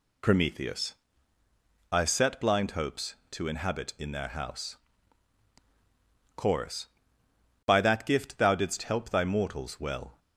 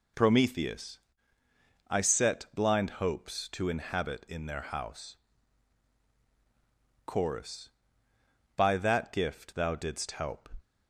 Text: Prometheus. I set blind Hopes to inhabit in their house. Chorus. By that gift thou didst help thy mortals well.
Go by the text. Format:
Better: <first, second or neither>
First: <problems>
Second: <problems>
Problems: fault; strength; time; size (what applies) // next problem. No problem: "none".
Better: first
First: none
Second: stops before "thy mortals well"; at 10.6 s